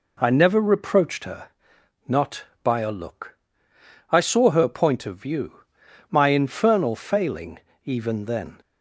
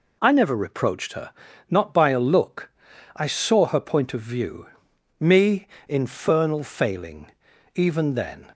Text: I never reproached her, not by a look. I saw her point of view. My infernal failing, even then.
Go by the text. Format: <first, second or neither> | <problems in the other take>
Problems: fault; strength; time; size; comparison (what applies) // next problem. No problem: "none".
first | says "Me" for "My"; at 5.2 s